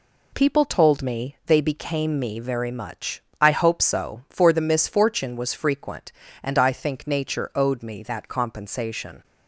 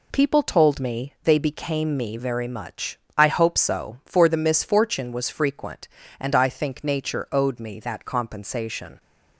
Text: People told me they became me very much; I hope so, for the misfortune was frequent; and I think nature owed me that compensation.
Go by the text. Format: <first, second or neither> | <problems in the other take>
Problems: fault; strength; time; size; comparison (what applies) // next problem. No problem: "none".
neither | none